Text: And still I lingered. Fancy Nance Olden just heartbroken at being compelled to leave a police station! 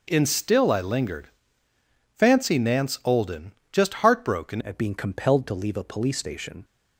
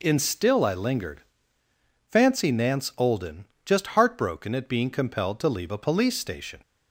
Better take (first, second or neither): second